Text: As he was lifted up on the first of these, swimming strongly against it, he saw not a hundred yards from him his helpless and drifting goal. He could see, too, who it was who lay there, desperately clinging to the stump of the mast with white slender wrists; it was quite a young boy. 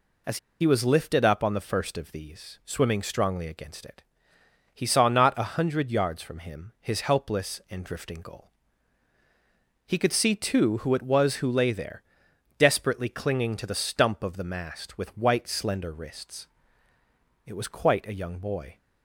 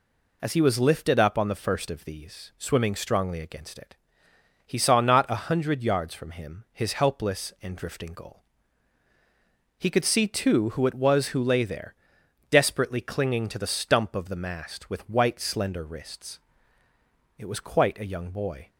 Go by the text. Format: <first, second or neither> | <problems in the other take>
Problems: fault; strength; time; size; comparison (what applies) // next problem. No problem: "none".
second | pauses between "As" and "he"; slight; at 0.3 s; 0.22 s long